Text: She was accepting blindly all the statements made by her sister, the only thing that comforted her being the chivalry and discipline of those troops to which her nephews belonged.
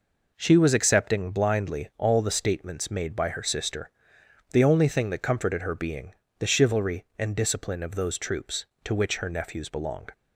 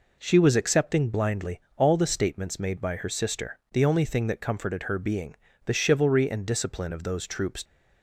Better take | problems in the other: first | pauses between "blindly" and "all"; slight; at 1.5 s; 0.16 s long // pauses between "being" and "the"; slight; at 5.3 s; 0.30 s long; slight in the first // stops before "to which her nephews belonged"; at 7.6 s

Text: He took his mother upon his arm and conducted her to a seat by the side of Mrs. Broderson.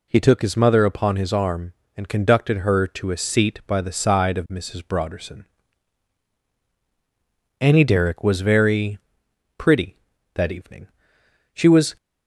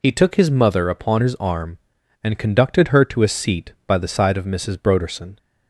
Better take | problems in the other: second | goes on to say "Annie Derrick was very pretty that evening She was"; strong; from 7.6 s on; 4.3 s long

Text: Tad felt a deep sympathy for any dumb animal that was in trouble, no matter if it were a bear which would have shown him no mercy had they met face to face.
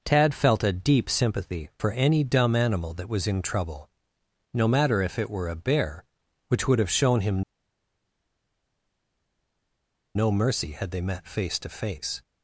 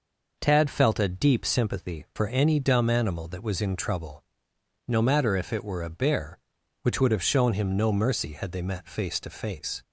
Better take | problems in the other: second | pauses between "him" and "no"; strong; at 7.4 s; 2.7 s long

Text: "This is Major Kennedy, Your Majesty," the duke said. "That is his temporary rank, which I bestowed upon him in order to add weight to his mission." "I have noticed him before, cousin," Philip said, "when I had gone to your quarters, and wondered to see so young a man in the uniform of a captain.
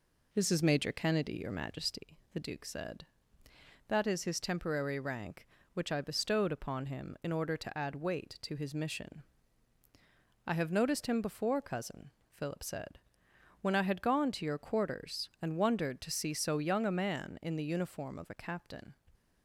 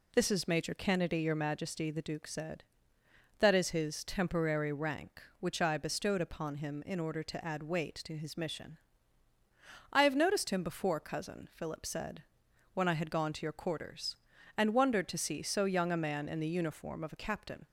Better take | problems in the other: second | starts louder than the rest; until 2.0 s; 3.5 dB

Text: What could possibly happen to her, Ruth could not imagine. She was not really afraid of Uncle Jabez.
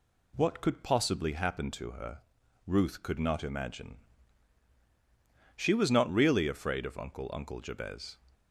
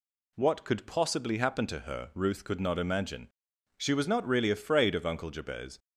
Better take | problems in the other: second | says "Uncle" twice; at 7.3 s

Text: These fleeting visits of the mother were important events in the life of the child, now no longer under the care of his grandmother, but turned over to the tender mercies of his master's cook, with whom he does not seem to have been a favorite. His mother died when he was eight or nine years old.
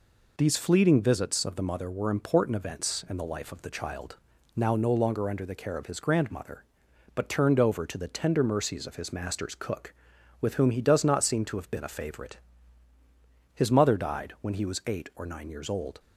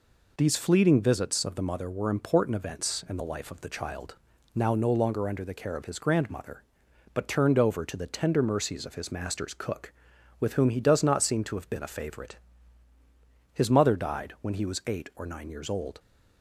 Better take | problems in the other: neither | none

